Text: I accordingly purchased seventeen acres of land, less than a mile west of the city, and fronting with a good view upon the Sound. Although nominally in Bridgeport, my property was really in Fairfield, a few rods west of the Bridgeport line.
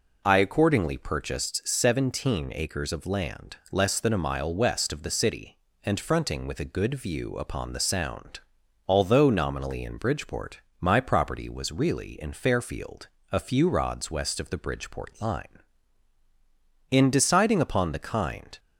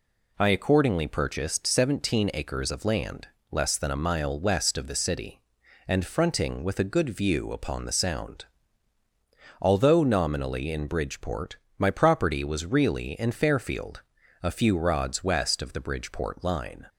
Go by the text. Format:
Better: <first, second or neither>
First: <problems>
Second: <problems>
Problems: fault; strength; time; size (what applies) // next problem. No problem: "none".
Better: second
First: goes on to say "In deciding upon the kind"; strong; from 16.9 s on; 1.6 s long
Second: none